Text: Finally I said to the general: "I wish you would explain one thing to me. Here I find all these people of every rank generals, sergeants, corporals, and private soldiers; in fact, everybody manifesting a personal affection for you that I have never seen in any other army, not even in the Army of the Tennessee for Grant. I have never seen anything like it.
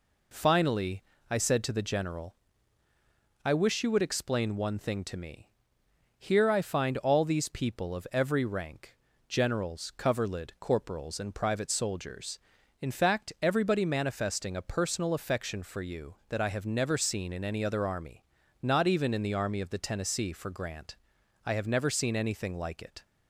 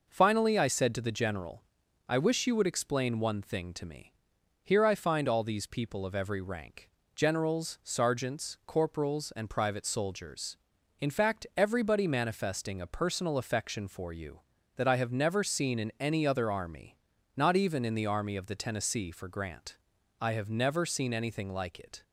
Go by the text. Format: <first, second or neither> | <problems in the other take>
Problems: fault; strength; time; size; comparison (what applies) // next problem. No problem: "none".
second | pauses between "Finally" and "I"; slight; at 1.0 s; 0.28 s long // pauses between "rank" and "generals"; slight; at 8.9 s; 0.32 s long; slight in the second // says "coverlid" for "sergeants"; at 9.9 s